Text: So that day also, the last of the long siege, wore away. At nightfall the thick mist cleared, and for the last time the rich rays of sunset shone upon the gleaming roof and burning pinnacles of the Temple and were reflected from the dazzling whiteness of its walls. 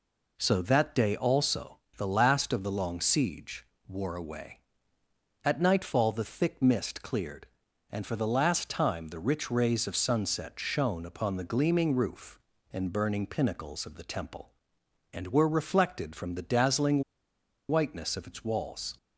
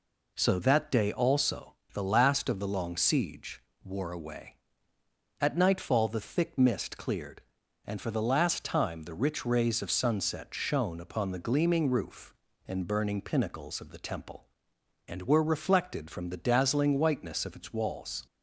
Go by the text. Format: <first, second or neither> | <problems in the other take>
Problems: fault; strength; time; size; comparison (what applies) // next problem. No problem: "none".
second | pauses between "dazzling" and "whiteness"; noticeable; at 17.0 s; 0.66 s long